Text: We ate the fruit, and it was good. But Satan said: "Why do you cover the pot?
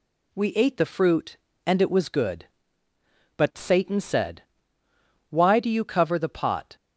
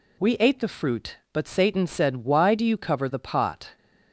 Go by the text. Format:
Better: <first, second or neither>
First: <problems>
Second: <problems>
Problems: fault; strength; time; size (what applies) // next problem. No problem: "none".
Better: first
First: none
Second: skips "and it was good"; at 1.2 s